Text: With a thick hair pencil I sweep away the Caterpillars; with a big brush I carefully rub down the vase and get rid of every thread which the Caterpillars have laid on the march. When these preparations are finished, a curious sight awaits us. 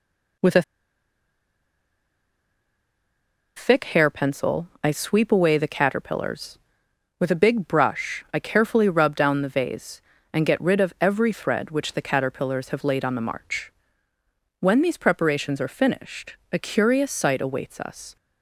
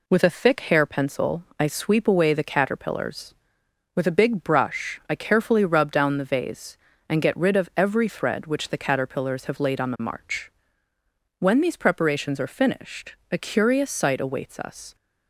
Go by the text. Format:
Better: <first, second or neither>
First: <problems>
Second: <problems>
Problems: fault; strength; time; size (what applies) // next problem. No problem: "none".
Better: second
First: pauses between "a" and "thick"; strong; at 0.6 s; 2.9 s long // pauses between "pencil" and "I"; slight; at 4.6 s; 0.16 s long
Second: pauses between "pencil" and "I"; slight; at 1.4 s; 0.16 s long